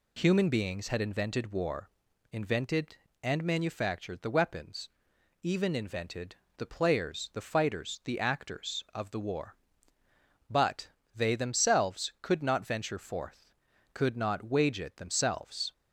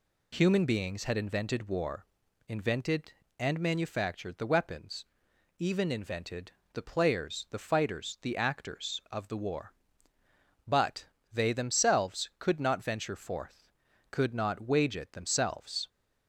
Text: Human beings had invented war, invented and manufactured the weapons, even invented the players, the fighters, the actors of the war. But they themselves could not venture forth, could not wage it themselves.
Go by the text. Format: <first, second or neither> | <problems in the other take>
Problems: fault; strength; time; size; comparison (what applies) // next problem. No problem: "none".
neither | pauses between "invented" and "the"; slight; the same in both // pauses between "But" and "they"; slight; the same in both